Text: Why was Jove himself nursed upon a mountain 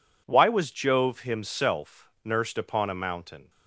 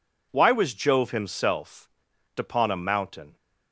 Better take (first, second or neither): first